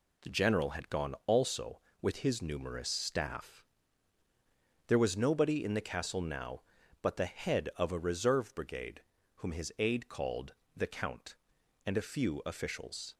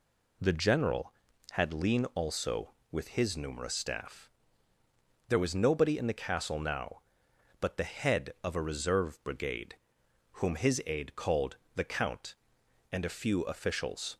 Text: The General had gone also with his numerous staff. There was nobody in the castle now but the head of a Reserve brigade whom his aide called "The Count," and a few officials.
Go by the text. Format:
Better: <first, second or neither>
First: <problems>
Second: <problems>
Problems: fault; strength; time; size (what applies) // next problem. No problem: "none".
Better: first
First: pauses between "brigade" and "whom"; slight; at 9.0 s; 0.34 s long // pauses between "called" and "The"; slight; at 10.5 s; 0.22 s long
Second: says "lean" for "gone"; at 1.7 s // pauses between "brigade" and "whom"; noticeable; at 9.7 s; 0.60 s long // pauses between "called" and "The"; slight; at 11.5 s; 0.18 s long